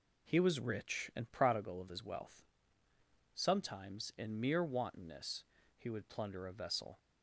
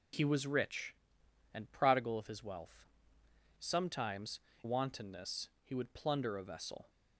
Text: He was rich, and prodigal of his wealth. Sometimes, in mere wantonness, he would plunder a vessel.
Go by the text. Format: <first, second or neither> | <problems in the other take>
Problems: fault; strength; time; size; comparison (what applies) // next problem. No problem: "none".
first | skips "in mere"; at 4.5 s